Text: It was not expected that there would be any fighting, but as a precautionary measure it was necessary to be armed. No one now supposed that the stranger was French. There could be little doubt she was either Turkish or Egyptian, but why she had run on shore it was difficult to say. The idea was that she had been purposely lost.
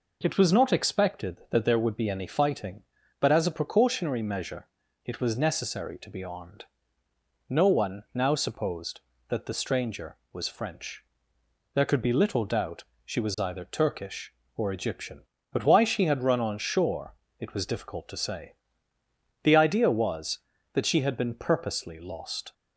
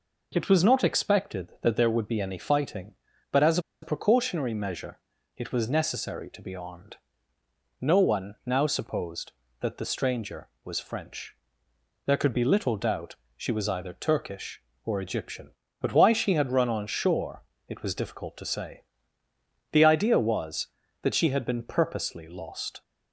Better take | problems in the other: first | pauses between "as" and "a"; slight; at 3.5 s; 0.23 s long // pauses between "measure" and "it"; slight; at 4.9 s; 0.36 s long; slight in the first // pauses between "doubt" and "she"; slight; at 13.1 s; 0.20 s long; slight in the first // pauses between "shore" and "it"; slight; at 17.4 s; 0.26 s long; slight in the first

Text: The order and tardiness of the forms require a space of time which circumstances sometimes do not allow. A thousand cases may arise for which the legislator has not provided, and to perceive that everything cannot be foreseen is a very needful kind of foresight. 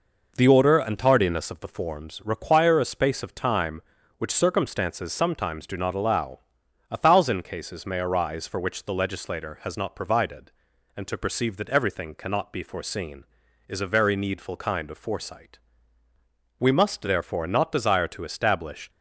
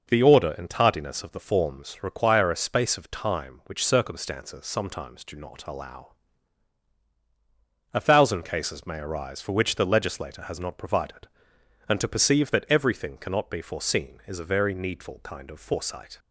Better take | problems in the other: second | goes on to say "We must therefore not desire to establish"; strong; from 16.5 s on; 2.3 s long

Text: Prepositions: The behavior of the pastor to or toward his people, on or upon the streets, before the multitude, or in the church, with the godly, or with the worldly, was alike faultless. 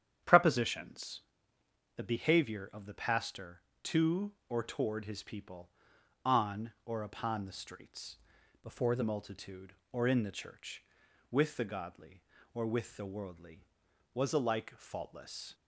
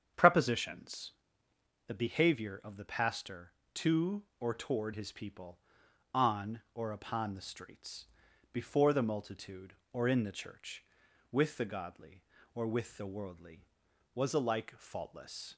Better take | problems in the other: second | starts louder than the rest; strong; until 2.0 s; 9 dB; strong in the second // changes voice from "before" to "the"; from 8.6 to 9.0 s; 0.4 s long

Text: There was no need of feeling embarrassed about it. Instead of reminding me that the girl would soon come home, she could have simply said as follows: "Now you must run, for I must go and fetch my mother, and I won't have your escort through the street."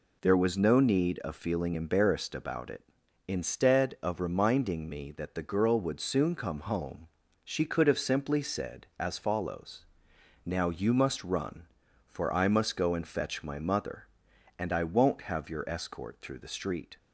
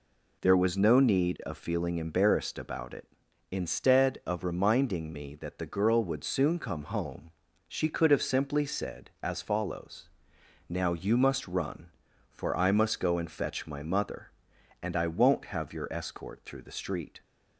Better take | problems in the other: neither | none

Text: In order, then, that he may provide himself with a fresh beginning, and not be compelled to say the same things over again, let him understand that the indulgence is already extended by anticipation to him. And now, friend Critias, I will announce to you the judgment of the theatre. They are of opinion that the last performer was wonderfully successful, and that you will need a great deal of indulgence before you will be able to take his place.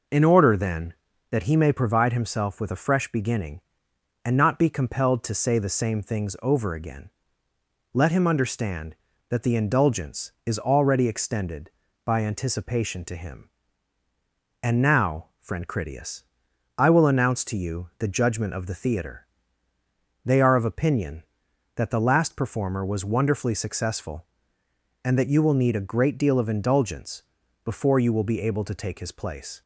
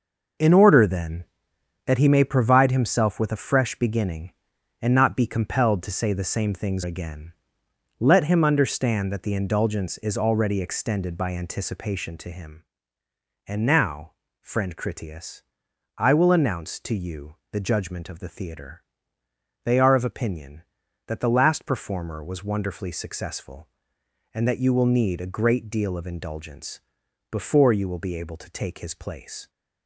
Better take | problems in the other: first | skips "over"; at 6.8 s // pauses between "you" and "the"; slight; at 17.3 s; 0.16 s long // pauses between "indulgence" and "before"; noticeable; at 26.7 s; 0.50 s long; also in the first

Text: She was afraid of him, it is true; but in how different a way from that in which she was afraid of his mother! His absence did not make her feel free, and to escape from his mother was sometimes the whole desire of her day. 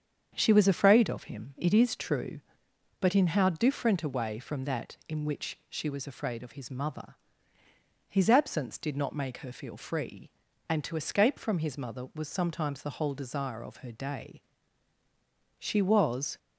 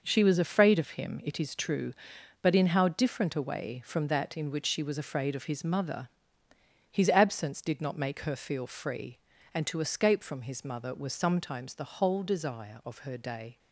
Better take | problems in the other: second | starts louder than the rest; strong; until 1.3 s; 7.5 dB // goes on to say "She was"; noticeable; from 15.5 s on; 0.78 s long

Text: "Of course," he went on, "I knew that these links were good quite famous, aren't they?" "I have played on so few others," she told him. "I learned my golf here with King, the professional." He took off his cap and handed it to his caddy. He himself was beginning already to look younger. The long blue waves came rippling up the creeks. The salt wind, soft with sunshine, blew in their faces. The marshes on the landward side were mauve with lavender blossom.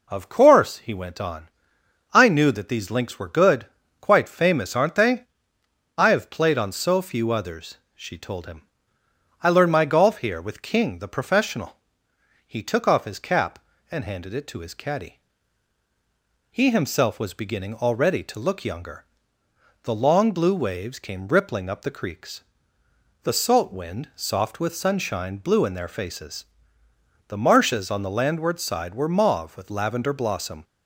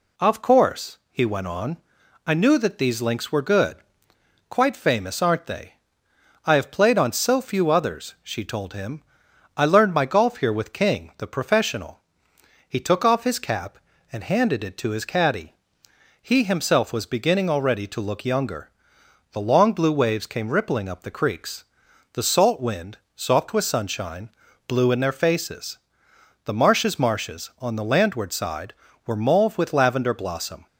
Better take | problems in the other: first | pauses between "good" and "quite"; noticeable; at 3.7 s; 0.72 s long; slight in the first // says "marshes" twice; at 26.9 s

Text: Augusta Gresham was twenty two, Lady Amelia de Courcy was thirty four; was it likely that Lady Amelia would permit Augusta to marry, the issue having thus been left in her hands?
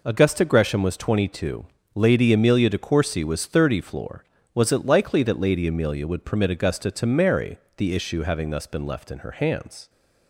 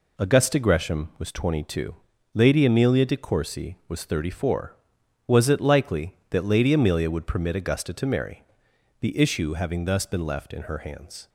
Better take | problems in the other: second | says "floor" for "four"; at 3.8 s

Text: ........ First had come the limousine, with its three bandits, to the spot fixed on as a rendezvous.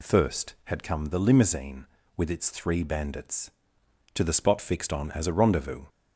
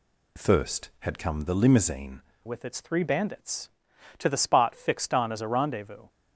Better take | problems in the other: first | changes voice at "with"; from 2.4 s on; 3.6 s long

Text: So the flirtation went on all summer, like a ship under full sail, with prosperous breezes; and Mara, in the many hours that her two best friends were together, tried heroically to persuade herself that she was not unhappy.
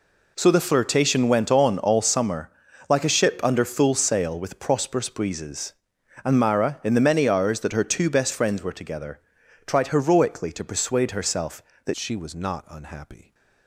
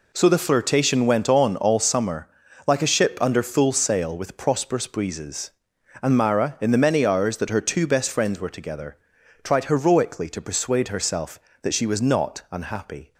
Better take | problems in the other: second | changes voice at "she"; from 11.9 s on; 1.4 s long

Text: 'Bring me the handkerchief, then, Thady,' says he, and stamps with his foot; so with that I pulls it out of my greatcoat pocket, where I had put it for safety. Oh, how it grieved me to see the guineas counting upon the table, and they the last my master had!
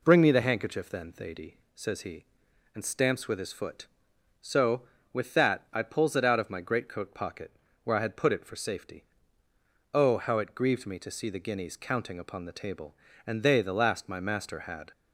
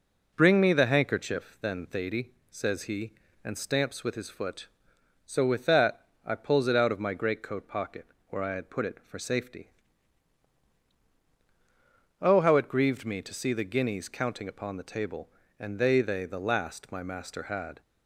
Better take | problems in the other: first | pauses between "that" and "I"; slight; at 6.0 s; 0.18 s long // says "they" twice; at 16.0 s

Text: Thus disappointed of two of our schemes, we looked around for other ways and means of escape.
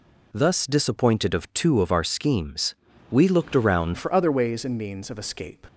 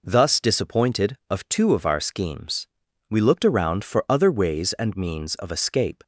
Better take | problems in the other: second | changes voice at "for"; from 3.9 s on; 1.7 s long

